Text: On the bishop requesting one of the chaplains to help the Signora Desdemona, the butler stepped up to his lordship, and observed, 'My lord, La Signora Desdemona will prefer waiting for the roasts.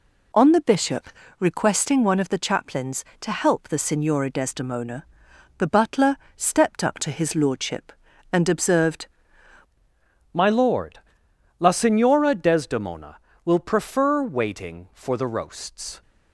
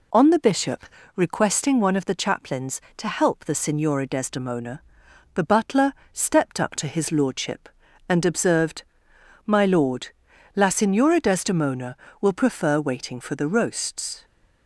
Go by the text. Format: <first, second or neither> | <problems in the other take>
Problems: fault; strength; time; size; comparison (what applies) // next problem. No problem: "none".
second | pauses between "bishop" and "requesting"; slight; at 1.0 s; 0.32 s long; slight in the second // pauses between "butler" and "stepped"; slight; at 6.1 s; 0.22 s long; slight in the second // changes voice at "My"; from 10.3 s on; 5.7 s long